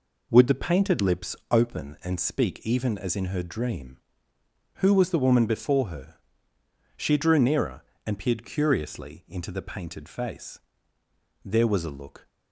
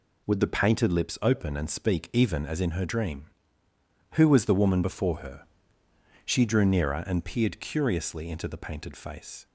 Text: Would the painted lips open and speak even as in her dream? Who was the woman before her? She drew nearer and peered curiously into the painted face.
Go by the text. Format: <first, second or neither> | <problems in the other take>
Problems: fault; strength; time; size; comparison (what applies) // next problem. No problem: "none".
second | pauses between "lips" and "open"; slight; at 1.3 s; 0.16 s long // goes on to say "There was a look"; noticeable; from 11.4 s on; 0.86 s long